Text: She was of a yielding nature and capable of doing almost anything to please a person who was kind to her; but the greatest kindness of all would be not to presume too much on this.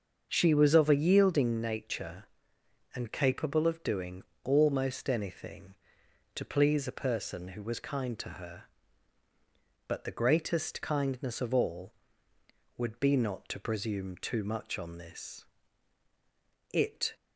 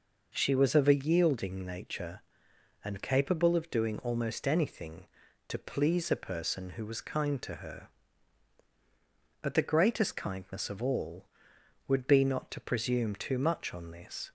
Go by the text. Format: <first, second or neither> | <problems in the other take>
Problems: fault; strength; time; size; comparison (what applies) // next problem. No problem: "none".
second | starts louder than the rest; until 1.3 s; 6.5 dB // pauses between "doing" and "almost"; slight; at 4.2 s; 0.22 s long // goes on to say "It"; slight; from 16.7 s on; 0.40 s long